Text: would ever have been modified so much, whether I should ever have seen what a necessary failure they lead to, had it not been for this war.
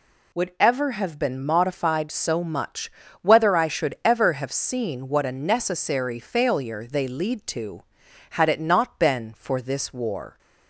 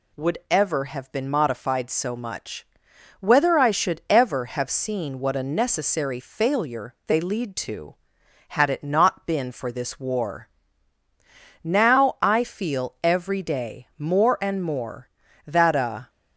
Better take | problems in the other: first | goes on to say "Now I feel every day more and more that a"; strong; from 11.6 s on; 4.4 s long

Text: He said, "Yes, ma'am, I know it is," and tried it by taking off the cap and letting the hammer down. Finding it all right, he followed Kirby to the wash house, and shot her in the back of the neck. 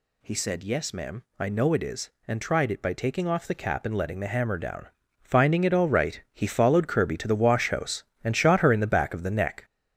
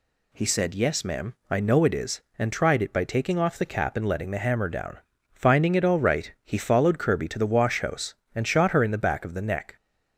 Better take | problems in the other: second | gets louder; throughout; 6.5 dB

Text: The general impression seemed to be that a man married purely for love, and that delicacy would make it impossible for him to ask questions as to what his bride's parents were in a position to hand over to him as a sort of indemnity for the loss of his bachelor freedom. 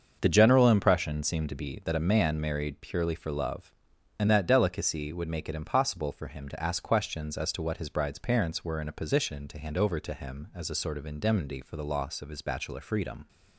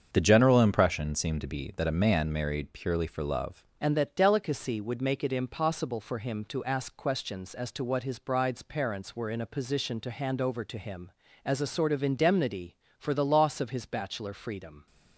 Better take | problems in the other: first | starts louder than the rest; strong; until 1.1 s; 7 dB; also in the first // changes voice at "and"; from 3.8 s on; 11.0 s long

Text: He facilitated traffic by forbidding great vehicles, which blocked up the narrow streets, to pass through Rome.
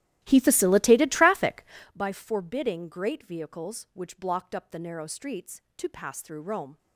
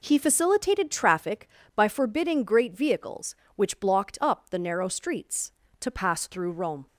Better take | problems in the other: second | starts louder than the rest; strong; until 1.9 s; 14 dB

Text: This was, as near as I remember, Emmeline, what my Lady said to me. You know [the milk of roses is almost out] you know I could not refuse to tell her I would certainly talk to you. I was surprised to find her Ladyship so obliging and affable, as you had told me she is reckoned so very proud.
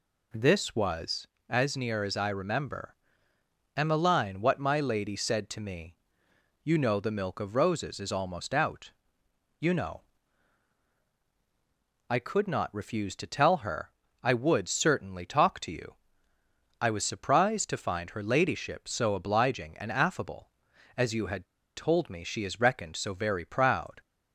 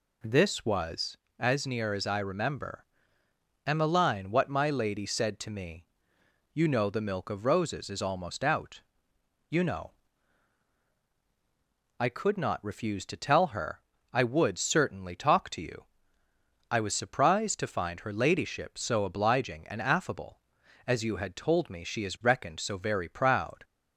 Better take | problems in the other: second | pauses between "out" and "you"; noticeable; at 8.9 s; 0.66 s long; noticeable in the second // pauses between "know" and "I"; strong; at 10.0 s; 2.1 s long; strong in the second // pauses between "her" and "I"; slight; at 13.9 s; 0.28 s long; slight in the second // pauses between "had" and "told"; slight; at 21.4 s; 0.29 s long

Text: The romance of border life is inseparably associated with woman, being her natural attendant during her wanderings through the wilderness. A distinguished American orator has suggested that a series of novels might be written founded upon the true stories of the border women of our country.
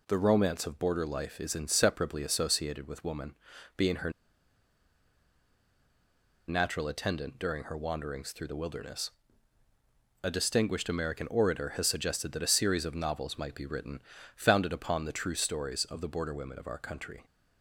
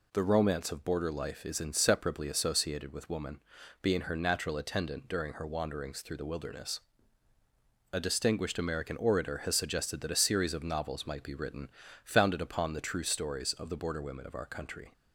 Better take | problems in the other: second | pauses between "her" and "natural"; strong; at 4.1 s; 2.3 s long // pauses between "written" and "founded"; slight; at 14.0 s; 0.34 s long; slight in the second

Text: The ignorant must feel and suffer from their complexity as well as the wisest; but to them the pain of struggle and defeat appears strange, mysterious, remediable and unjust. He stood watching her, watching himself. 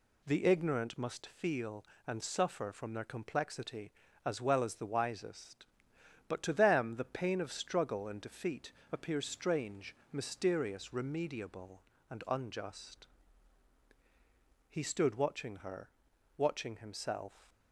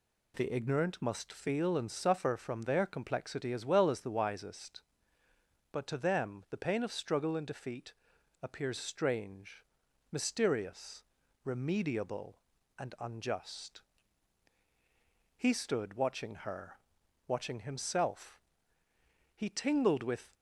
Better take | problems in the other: first | pauses between "defeat" and "appears"; noticeable; at 7.9 s; 0.48 s long; slight in the first // goes on to say "He tingled with"; noticeable; from 19.3 s on; 0.98 s long

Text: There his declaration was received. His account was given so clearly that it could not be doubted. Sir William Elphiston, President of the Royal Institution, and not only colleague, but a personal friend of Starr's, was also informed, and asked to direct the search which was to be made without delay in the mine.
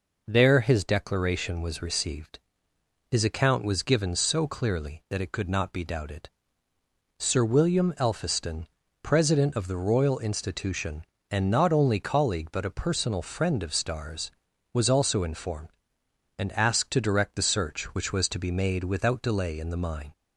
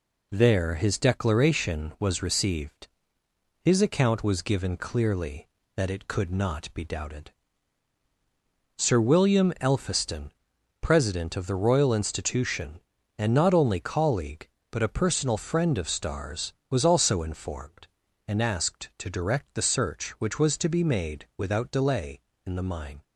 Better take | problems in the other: first | skips "so"; at 4.7 s

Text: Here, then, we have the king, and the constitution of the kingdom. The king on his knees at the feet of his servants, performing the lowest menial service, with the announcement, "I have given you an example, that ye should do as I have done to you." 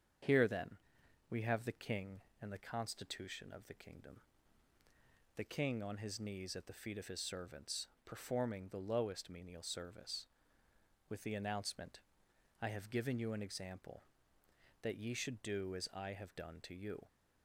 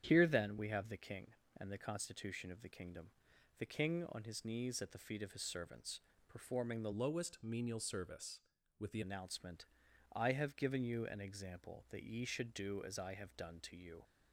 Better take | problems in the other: first | starts louder than the rest; strong; until 1.0 s; 9.5 dB; strong in the first // changes voice from "lowest" to "the"; from 6.9 to 8.9 s; 2.0 s long

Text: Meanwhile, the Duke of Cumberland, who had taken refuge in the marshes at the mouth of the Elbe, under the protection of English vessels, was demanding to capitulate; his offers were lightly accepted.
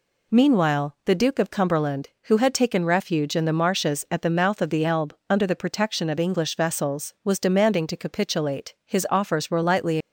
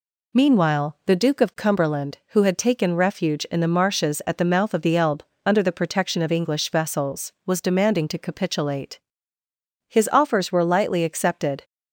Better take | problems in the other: second | stops before "accepted"; at 10.0 s

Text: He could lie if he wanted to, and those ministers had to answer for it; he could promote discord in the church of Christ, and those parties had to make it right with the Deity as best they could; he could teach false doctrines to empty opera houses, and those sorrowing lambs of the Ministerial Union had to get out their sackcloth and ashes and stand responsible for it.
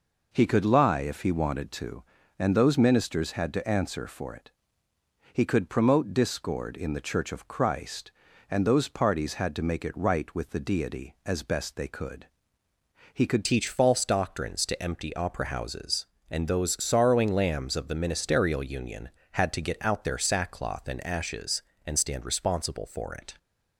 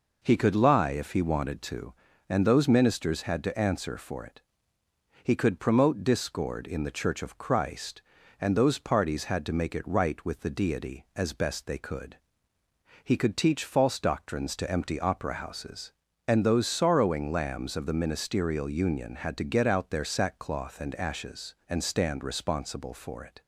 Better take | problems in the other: second | changes voice at "teach"; from 13.4 s on; 9.9 s long

